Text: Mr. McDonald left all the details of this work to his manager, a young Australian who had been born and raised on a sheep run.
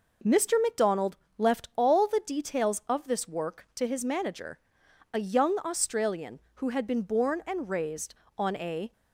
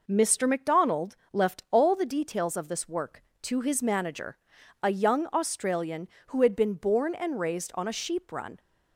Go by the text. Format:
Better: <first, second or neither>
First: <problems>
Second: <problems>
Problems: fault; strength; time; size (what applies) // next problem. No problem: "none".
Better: second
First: pauses between "McDonald" and "left"; slight; at 1.1 s; 0.20 s long // stops before "sheep run"; at 8.9 s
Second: pauses between "McDonald" and "left"; slight; at 1.1 s; 0.16 s long